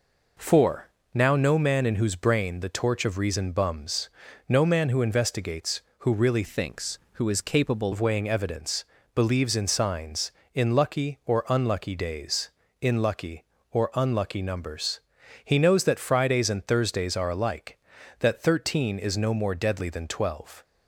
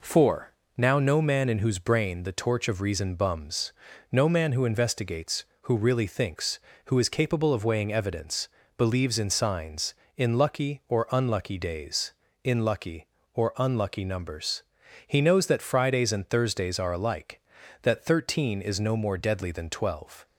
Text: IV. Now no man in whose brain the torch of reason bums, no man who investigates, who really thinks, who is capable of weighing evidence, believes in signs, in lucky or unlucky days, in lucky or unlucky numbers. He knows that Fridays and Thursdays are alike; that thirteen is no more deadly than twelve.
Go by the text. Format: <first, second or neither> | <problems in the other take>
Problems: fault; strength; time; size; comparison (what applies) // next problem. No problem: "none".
second | changes voice from "thinks" to "capable"; from 6.4 to 7.9 s; 1.5 s long